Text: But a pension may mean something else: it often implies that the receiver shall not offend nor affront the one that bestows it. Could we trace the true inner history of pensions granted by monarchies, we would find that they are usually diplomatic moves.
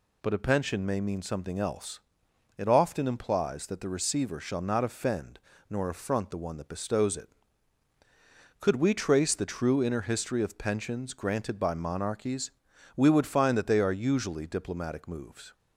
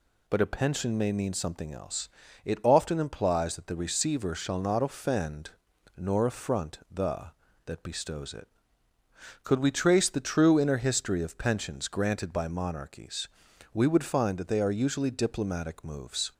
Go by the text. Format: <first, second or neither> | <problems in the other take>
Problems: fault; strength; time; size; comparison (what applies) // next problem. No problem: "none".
first | pauses between "offend" and "nor"; noticeable; at 5.5 s; 0.46 s long; slight in the first // skips "one"; at 7.4 s